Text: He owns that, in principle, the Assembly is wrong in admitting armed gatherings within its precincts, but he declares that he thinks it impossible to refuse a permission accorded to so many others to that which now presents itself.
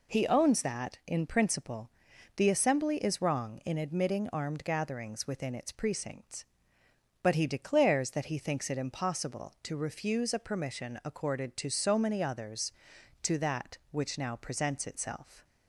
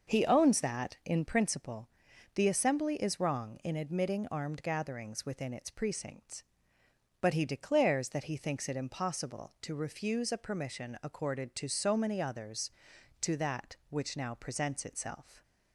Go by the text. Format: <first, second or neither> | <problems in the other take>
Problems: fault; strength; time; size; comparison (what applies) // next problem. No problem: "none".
first | starts louder than the rest; noticeable; until 1.4 s; 6 dB